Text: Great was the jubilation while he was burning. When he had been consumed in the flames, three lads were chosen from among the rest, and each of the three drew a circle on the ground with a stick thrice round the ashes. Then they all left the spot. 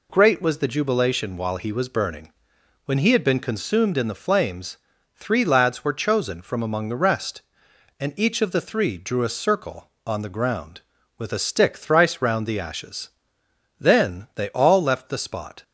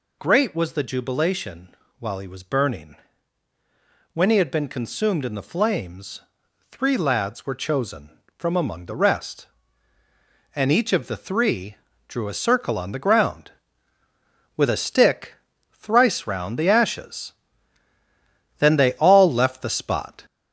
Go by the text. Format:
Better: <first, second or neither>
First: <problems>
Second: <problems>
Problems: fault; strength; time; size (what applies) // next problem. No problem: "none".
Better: first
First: none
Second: gets louder; noticeable; throughout; 5 dB // pauses between "jubilation" and "while"; slight; at 1.7 s; 0.26 s long // pauses between "three" and "drew"; slight; at 11.7 s; 0.32 s long // pauses between "stick" and "thrice"; slight; at 15.3 s; 0.36 s long